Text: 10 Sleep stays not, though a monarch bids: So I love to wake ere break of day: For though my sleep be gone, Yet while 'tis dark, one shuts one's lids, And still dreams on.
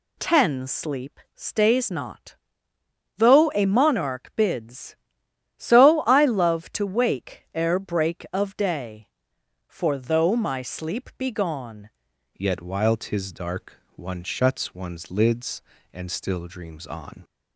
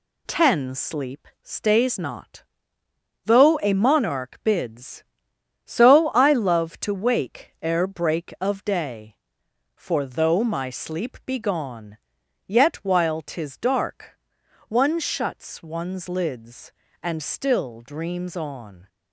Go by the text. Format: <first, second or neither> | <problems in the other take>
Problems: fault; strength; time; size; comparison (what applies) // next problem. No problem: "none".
second | pauses between "Sleep" and "stays"; slight; at 1.1 s; 0.16 s long; slight in the second // changes voice at "Yet"; from 12.3 s on; 4.9 s long